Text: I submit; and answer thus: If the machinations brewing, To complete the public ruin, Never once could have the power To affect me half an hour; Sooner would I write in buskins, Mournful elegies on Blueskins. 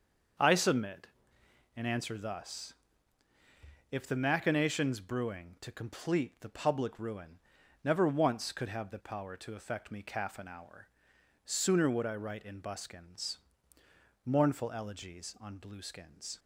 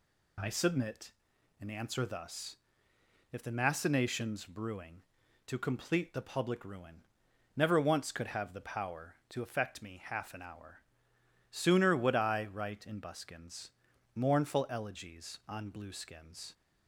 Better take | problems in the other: second | starts louder than the rest; until 2.0 s; 6.5 dB // says "calf" for "half"; at 10.0 s

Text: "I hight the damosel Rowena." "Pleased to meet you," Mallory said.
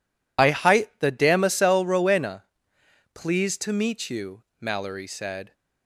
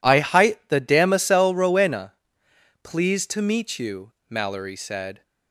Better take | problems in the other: second | loses the start of "I"; at 0.3 s; 45 ms

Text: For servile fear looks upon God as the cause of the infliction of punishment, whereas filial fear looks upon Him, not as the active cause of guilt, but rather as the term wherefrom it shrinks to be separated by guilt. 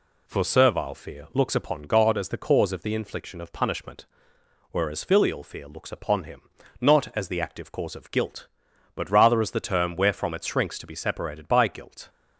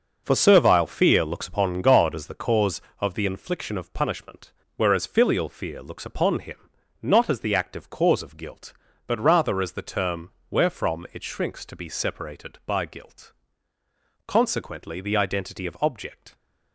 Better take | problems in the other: first | pauses between "term" and "wherefrom"; slight; at 10.3 s; 0.18 s long // goes on to say "Consequently the identity of object"; strong; from 14.2 s on; 2.0 s long

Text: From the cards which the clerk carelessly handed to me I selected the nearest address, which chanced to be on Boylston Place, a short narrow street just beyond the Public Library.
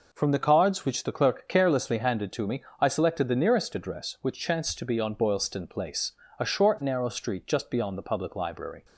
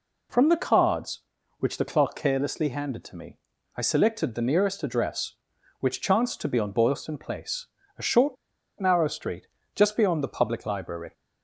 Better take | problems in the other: first | pauses between "me" and "I"; at 3.3 s; 0.38 s long; slight in the first // pauses between "short" and "narrow"; at 8.3 s; 0.45 s long // pauses between "street" and "just"; slight; at 9.4 s; 0.28 s long

